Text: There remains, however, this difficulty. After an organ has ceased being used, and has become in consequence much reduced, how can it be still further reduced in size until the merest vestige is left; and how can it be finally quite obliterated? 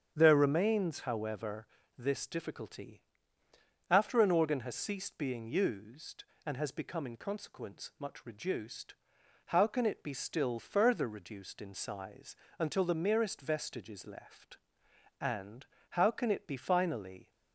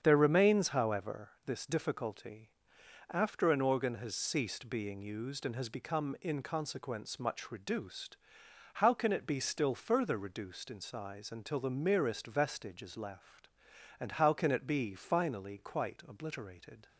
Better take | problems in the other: second | starts louder than the rest; strong; until 1.1 s; 8 dB; strong in the second // pauses between "size" and "until"; slight; at 12.3 s; 0.24 s long // pauses between "and" and "how"; slight; at 15.6 s; 0.24 s long // stops before "quite obliterated"; at 17.3 s

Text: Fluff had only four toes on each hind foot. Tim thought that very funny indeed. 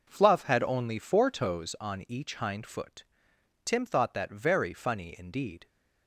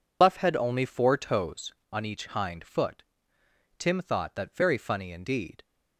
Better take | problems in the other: first | loses the start of "Fluff"; at 0.2 s; 105 ms

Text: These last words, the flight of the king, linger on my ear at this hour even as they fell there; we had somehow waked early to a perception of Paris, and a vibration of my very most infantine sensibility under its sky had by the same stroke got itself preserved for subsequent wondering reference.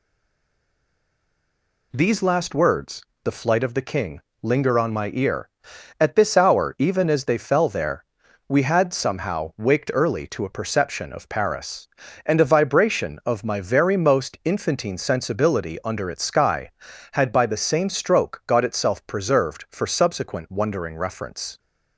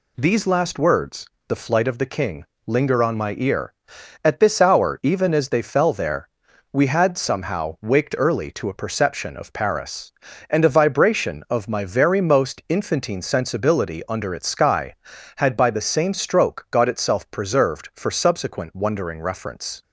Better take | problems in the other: second | stays silent before the first word; noticeable; until 1.9 s; 1.9 s long

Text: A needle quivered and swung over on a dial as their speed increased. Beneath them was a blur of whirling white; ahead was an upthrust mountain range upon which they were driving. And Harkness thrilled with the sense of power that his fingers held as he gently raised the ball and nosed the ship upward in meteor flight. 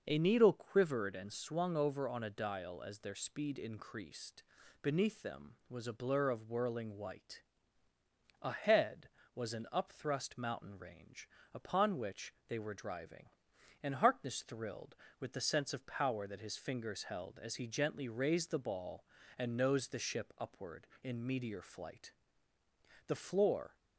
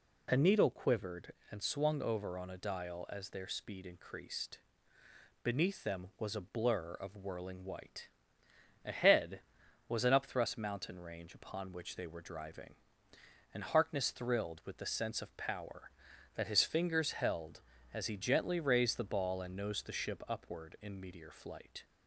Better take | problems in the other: second | pauses between "range" and "upon"; slight; at 11.2 s; 0.24 s long // pauses between "which" and "they"; slight; at 12.3 s; 0.16 s long // goes on to say "The floor"; noticeable; from 23.0 s on; 0.68 s long

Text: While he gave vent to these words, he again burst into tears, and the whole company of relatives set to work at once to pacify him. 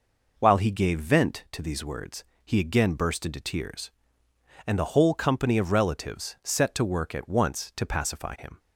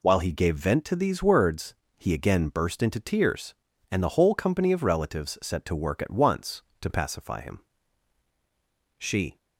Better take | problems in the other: first | goes on to say "She"; slight; from 8.9 s on; 0.40 s long

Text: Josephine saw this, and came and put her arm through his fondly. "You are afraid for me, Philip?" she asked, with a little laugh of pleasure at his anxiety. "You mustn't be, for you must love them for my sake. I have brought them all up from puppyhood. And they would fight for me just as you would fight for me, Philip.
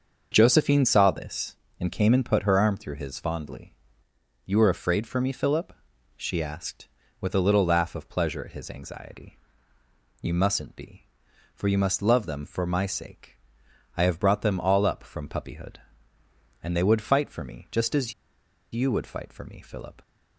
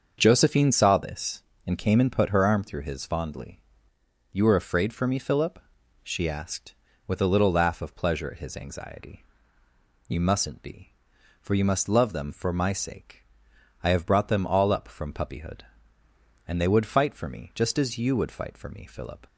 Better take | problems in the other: second | starts louder than the rest; until 1.3 s; 6.5 dB; also in the second // pauses between "as" and "you"; noticeable; at 18.1 s; 0.60 s long

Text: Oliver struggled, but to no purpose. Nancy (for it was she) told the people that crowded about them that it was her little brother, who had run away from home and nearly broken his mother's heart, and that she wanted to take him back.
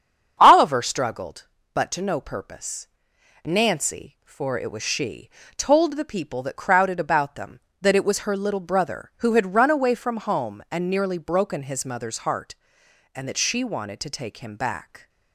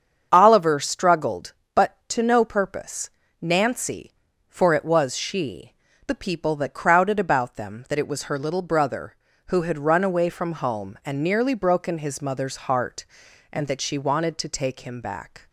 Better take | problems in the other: first | starts louder than the rest; strong; until 1.3 s; 7 dB; strong in the first // skips "told"; at 5.9 s

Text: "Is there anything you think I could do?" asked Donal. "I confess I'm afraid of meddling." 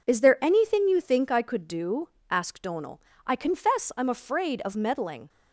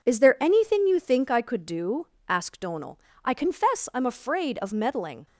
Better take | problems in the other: neither | none

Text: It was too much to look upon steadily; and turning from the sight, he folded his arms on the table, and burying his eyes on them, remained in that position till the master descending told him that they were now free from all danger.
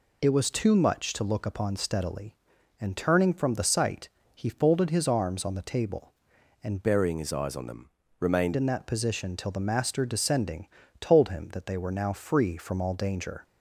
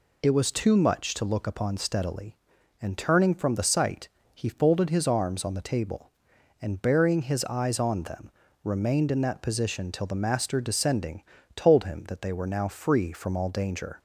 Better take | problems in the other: second | changes voice from "burying" to "remained"; from 6.8 to 8.5 s; 1.7 s long // pauses between "descending" and "told"; slight; at 10.6 s; 0.32 s long; slight in the second

